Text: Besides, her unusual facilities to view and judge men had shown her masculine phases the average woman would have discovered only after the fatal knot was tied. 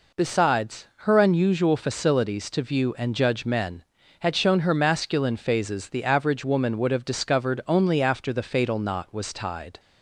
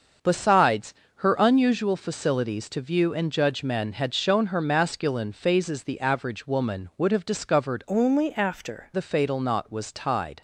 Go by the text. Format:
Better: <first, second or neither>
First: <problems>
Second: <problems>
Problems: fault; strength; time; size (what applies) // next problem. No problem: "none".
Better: first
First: none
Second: starts louder than the rest; until 1.5 s; 6.5 dB // changes voice from "only" to "after"; from 7.8 to 8.9 s; 1.1 s long